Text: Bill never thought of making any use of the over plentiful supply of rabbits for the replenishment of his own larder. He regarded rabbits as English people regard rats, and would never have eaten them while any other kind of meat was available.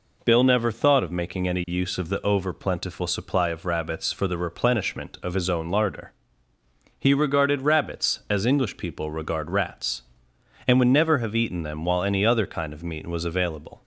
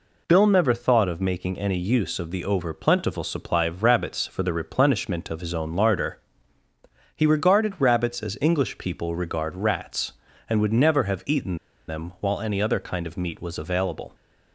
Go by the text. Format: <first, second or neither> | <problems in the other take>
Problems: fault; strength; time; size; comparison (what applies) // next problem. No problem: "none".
first | pauses between "eaten" and "them"; slight; at 11.5 s; 0.30 s long